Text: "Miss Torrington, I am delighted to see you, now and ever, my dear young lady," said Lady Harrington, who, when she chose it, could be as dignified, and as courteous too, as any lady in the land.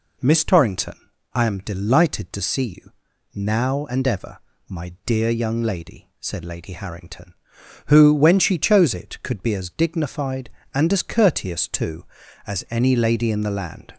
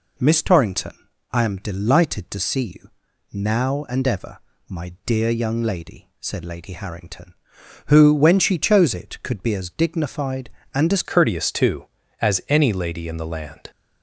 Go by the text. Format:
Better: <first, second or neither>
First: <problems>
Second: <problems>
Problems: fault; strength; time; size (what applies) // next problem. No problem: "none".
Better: first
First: none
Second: changes voice at "courteous"; from 11.0 s on; 2.7 s long